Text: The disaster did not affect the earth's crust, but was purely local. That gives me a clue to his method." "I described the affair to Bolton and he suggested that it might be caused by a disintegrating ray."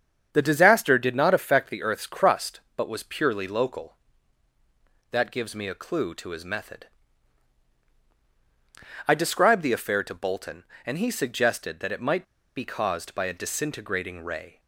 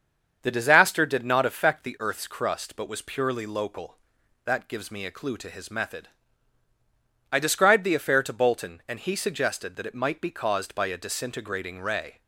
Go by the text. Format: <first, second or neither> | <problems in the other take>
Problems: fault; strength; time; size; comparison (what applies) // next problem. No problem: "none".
second | starts louder than the rest; strong; until 1.3 s; 7.5 dB; also in the second // pauses between "might" and "be"; slight; at 12.2 s; 0.33 s long